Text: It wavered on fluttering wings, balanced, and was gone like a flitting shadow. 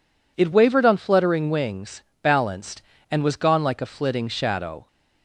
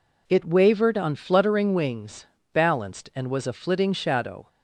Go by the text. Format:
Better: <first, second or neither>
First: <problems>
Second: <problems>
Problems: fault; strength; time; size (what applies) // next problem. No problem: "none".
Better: first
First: none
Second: skips "gone like"; at 3.4 s